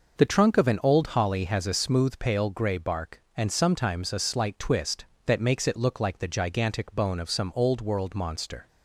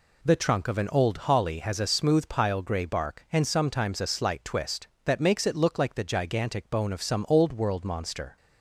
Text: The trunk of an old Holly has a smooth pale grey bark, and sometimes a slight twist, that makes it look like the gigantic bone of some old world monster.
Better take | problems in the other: first | says "pile" for "pale"; at 2.2 s

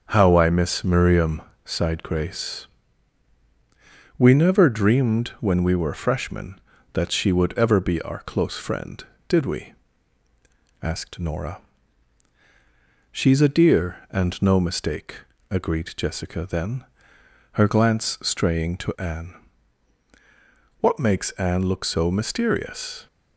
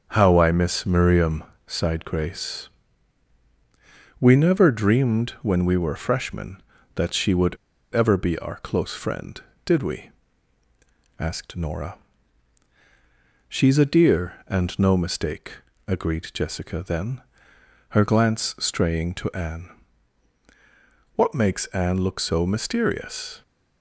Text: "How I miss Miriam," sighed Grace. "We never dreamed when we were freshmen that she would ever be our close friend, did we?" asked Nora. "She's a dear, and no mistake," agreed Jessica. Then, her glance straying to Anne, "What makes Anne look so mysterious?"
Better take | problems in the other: first | starts louder than the rest; until 1.1 s; 7 dB; also in the first // pauses between "would" and "ever"; at 7.5 s; 0.36 s long

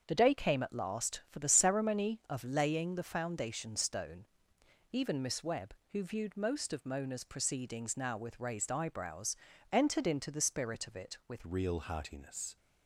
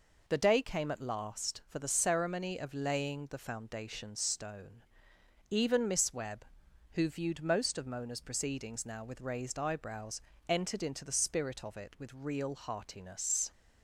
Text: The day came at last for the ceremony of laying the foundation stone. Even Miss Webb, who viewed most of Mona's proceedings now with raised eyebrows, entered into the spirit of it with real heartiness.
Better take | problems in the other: second | starts louder than the rest; until 1.0 s; 7 dB // changes voice at "real"; from 11.4 s on; 1.1 s long

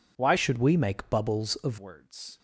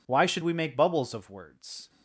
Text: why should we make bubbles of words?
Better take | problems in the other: second | changes voice from "should" to "of"; from 0.3 to 1.7 s; 1.4 s long

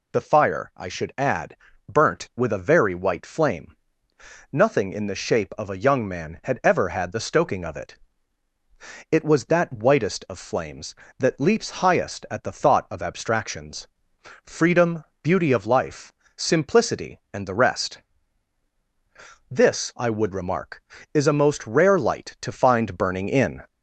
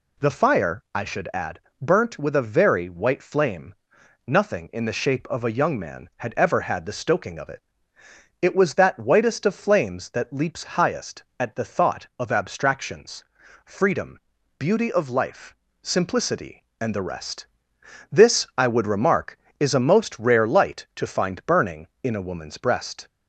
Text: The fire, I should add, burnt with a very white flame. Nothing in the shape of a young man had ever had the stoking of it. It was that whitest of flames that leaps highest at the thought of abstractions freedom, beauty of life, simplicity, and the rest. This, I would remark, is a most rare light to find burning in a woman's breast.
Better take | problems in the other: second | pauses between "abstractions" and "freedom"; noticeable; at 13.8 s; 0.56 s long; also in the second // stops before "a woman's breast"; at 23.6 s

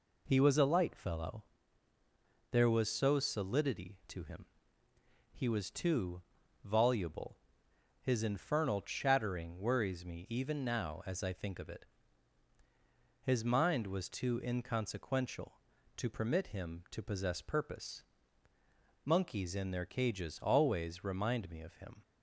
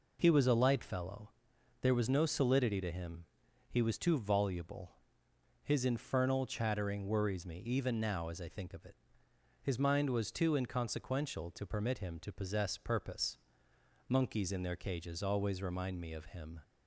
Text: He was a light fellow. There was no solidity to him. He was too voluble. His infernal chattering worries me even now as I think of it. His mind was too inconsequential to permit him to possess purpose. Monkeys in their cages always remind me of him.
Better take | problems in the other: second | says "so" for "no"; at 2.9 s // pauses between "too" and "voluble"; at 6.2 s; 0.44 s long

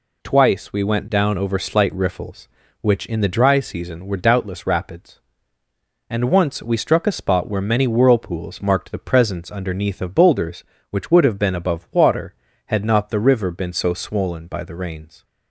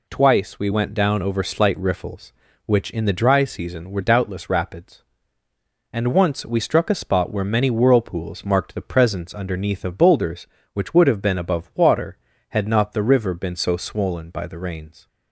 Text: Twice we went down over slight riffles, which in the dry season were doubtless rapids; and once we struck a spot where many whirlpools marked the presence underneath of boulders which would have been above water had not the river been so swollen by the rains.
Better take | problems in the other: neither | none

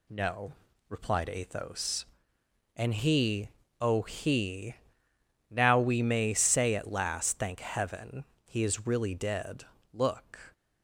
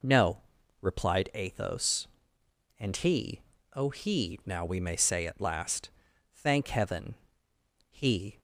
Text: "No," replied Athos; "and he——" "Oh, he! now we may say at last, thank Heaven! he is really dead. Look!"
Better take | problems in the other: first | stops before "is really dead Look"; at 8.3 s

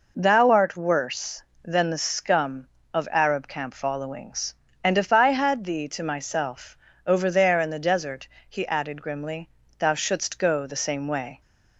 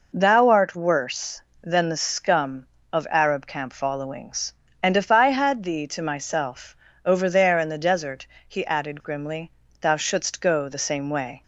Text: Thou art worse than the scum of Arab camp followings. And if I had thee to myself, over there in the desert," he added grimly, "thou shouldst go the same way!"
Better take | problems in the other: neither | none

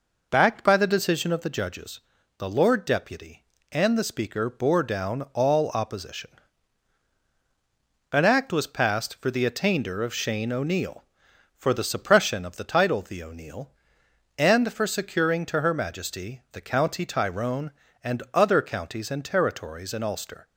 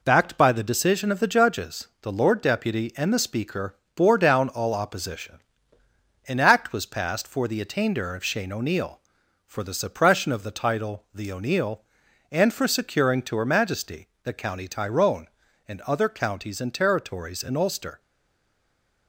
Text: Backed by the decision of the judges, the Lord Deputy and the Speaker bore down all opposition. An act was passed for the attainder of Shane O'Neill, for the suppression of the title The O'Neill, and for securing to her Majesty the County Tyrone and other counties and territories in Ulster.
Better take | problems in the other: first | pauses between "Speaker" and "bore"; slight; at 3.7 s; 0.20 s long // pauses between "Majesty" and "the"; slight; at 14.0 s; 0.16 s long // stays silent after the last word; from 17.9 s on; 1.1 s long

